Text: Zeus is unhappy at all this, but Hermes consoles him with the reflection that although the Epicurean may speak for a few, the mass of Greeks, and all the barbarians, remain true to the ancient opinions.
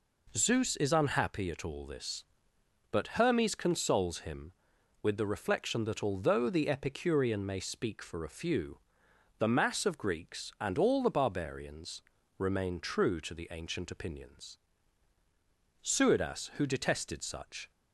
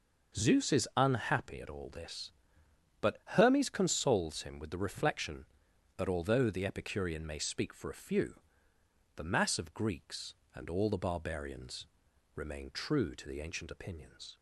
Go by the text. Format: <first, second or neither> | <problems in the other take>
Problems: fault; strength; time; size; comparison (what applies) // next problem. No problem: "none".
second | goes on to say "Suidas who detested such"; strong; from 15.8 s on; 1.8 s long